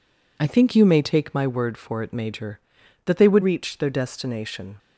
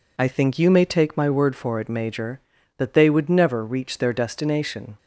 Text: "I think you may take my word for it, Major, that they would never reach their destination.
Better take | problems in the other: second | skips "never"; at 3.4 s

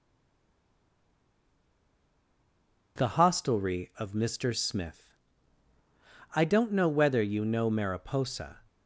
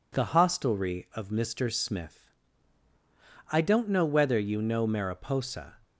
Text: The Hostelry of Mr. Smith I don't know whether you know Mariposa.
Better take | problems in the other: second | stays silent before the first word; strong; until 2.9 s; 2.9 s long // pauses between "Smith" and "I"; at 5.1 s; 1.2 s long; also in the second

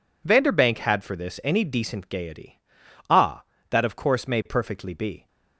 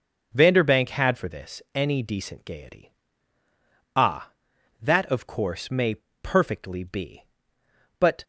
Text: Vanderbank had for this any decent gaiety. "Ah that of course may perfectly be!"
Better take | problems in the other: first | starts louder than the rest; until 1.3 s; 6.5 dB // pauses between "may" and "perfectly"; slight; at 5.9 s; 0.25 s long // goes on to say "But"; slight; from 7.9 s on; 0.24 s long

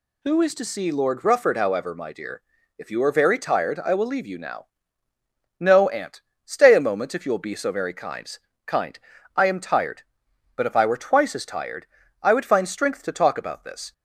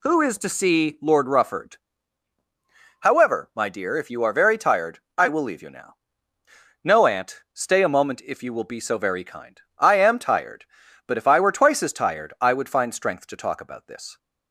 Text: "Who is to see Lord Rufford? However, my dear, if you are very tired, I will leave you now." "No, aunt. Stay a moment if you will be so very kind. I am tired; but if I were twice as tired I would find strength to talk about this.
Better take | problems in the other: second | says "kind" twice; at 8.6 s // pauses between "tired" and "I"; at 11.8 s; 0.38 s long

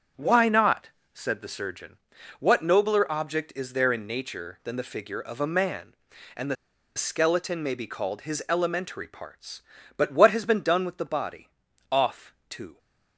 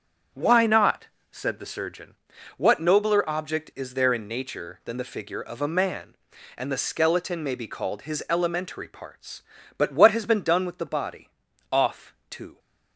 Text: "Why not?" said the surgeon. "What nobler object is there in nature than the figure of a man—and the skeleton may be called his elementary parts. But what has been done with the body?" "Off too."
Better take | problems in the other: second | starts louder than the rest; strong; until 1.3 s; 7.5 dB; strong in the second // pauses between "the" and "skeleton"; at 6.5 s; 0.40 s long // pauses between "Off" and "too"; slight; at 12.3 s; 0.16 s long; slight in the second

